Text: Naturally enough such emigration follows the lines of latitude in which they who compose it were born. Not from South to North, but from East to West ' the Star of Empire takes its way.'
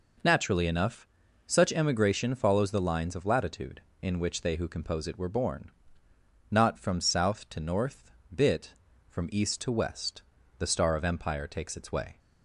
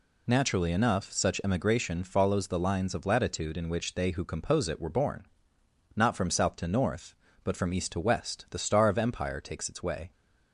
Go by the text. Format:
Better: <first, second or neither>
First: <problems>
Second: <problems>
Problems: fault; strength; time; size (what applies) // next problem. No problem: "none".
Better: second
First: pauses between "enough" and "such"; at 1.0 s; 0.40 s long // says "bit" for "but"; at 8.3 s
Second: none